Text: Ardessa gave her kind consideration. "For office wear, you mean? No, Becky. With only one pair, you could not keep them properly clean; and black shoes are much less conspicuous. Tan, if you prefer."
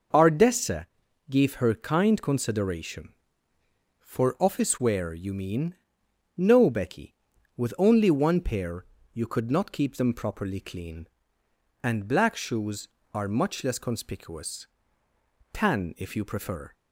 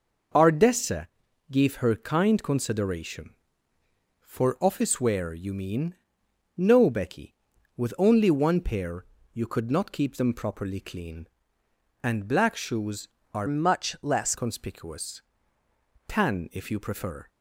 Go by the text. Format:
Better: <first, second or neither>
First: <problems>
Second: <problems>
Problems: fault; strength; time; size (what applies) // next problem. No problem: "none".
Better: first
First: pauses between "Ardessa" and "gave"; at 0.8 s; 0.42 s long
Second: pauses between "Ardessa" and "gave"; at 1.0 s; 0.42 s long // changes voice from "much" to "less"; from 13.4 to 14.3 s; 0.9 s long